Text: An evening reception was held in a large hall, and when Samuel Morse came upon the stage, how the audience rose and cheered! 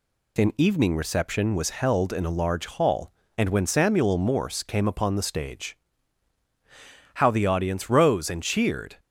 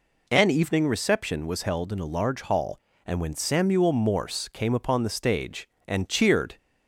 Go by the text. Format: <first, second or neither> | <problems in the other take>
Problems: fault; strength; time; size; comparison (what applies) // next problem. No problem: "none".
first | skips "how the audience rose"; at 5.7 s